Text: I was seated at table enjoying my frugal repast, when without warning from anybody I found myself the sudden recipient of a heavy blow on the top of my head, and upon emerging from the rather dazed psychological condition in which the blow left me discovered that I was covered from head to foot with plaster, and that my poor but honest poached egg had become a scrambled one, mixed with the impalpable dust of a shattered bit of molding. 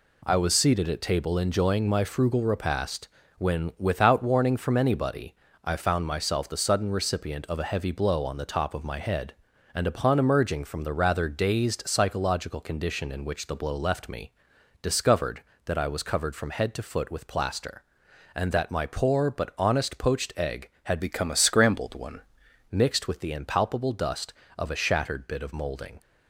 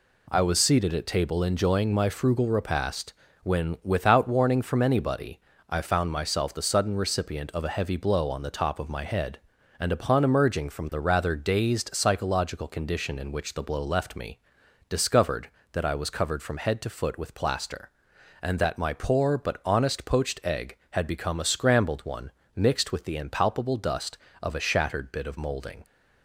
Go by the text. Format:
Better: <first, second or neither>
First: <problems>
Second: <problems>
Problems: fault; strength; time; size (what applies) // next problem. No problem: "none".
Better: second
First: pauses between "anybody" and "I"; slight; at 5.3 s; 0.30 s long // pauses between "me" and "discovered"; noticeable; at 14.3 s; 0.50 s long // changes voice from "become" to "one"; from 20.9 to 22.1 s; 1.2 s long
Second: pauses between "anybody" and "I"; slight; at 5.4 s; 0.30 s long // pauses between "me" and "discovered"; noticeable; at 14.3 s; 0.50 s long